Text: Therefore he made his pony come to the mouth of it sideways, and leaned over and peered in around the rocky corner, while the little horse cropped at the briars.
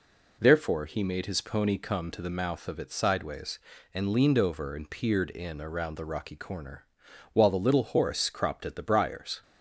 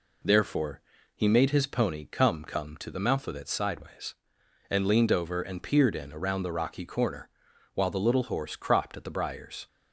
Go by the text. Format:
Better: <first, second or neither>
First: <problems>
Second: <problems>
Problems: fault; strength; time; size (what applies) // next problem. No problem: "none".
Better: first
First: none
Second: pauses between "Therefore" and "he"; slight; at 0.8 s; 0.34 s long // says "come" twice; at 2.4 s